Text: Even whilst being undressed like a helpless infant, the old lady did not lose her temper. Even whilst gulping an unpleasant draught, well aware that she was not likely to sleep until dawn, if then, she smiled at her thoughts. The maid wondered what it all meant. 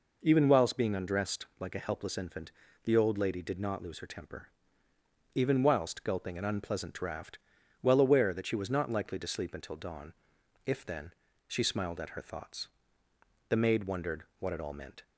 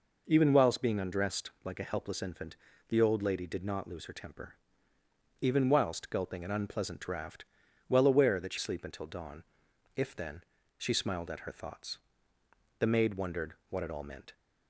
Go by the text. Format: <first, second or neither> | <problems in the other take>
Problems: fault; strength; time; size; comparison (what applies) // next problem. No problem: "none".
first | skips "was not likely to"; at 8.5 s // pauses between "wondered" and "what"; slight; at 13.5 s; 0.16 s long; slight in the first